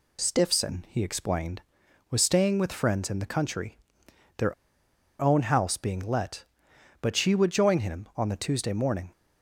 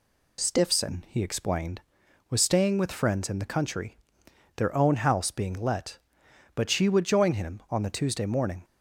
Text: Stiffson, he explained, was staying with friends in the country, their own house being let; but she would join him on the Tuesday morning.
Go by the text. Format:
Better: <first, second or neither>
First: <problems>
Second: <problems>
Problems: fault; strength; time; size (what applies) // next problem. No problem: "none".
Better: second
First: pauses between "their" and "own"; noticeable; at 4.5 s; 0.66 s long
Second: none